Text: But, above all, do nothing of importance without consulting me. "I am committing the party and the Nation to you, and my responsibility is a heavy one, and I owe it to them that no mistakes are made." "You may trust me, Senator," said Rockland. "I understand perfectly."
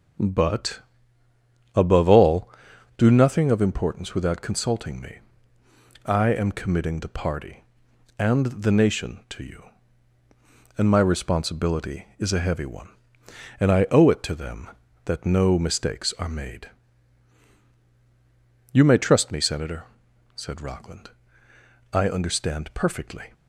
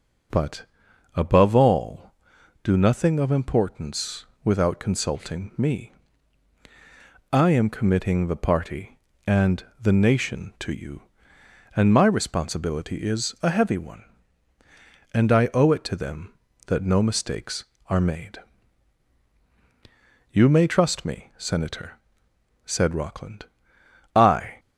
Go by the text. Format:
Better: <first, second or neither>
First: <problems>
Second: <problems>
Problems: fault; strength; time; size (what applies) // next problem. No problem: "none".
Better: first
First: none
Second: pauses between "importance" and "without"; slight; at 4.2 s; 0.18 s long // pauses between "and" and "the"; slight; at 9.6 s; 0.16 s long // stops before "understand perfectly"; at 24.5 s